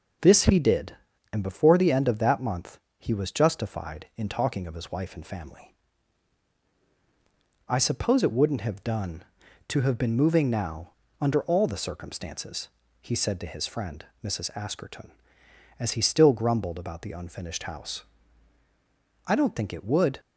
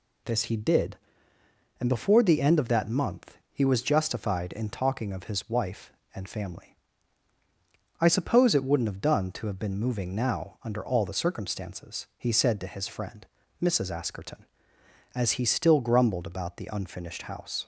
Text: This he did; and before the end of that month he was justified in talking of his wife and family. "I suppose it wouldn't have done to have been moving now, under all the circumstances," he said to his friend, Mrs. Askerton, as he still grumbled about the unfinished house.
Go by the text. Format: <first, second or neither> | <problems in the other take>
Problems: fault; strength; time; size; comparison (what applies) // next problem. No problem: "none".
second | pauses between "month" and "he"; slight; at 2.7 s; 0.20 s long // goes on to say "I don't think it would"; noticeable; from 19.2 s on; 0.94 s long